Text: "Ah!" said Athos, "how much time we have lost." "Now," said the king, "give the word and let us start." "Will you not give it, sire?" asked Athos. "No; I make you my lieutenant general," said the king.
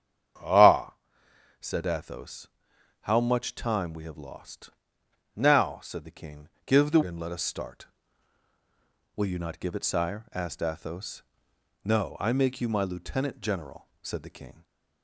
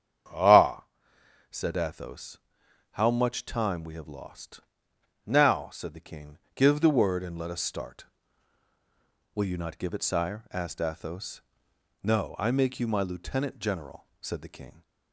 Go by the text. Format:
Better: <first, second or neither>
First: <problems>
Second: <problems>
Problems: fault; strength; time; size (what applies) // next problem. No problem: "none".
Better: second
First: starts louder than the rest; strong; until 2.0 s; 8.5 dB // skips "word"; at 7.0 s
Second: starts louder than the rest; strong; until 1.9 s; 8 dB